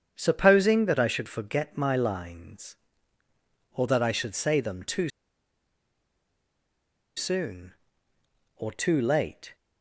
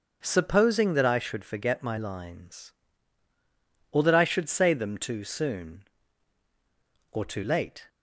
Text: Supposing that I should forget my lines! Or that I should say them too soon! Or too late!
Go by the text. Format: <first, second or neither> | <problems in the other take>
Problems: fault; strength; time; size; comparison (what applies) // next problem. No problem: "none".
second | starts louder than the rest; strong; until 1.1 s; 8 dB; also in the second // pauses between "too" and "soon"; strong; at 5.0 s; 2.0 s long